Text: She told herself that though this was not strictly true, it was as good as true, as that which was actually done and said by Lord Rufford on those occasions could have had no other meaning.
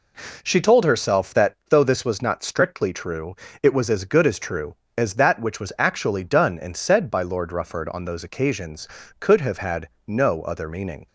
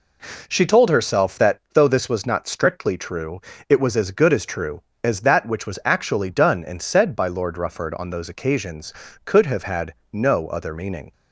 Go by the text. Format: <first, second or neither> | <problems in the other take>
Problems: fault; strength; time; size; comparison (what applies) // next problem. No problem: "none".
neither | pauses between "had" and "no"; slight; the same in both